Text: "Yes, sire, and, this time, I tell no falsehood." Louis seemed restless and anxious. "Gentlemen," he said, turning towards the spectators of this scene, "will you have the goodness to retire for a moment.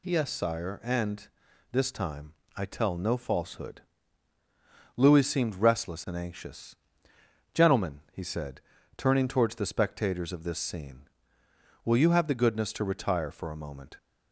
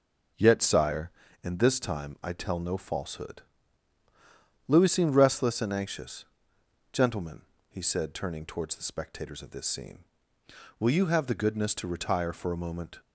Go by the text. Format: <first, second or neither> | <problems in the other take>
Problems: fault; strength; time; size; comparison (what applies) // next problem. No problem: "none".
first | says "Yet" for "Yes"; at 0.3 s